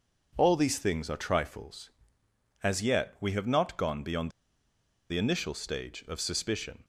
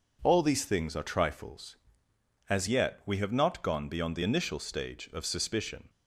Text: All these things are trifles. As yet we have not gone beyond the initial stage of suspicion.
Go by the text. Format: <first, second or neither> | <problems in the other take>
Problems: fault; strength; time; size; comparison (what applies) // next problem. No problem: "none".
second | pauses between "beyond" and "the"; noticeable; at 4.3 s; 0.78 s long